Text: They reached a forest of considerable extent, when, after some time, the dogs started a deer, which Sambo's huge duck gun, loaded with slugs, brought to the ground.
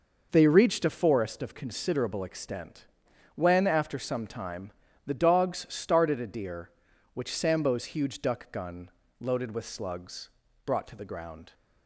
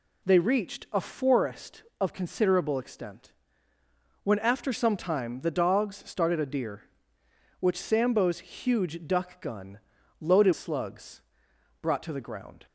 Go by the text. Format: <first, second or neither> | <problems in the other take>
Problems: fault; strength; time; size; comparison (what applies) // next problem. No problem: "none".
first | skips "with"; at 10.5 s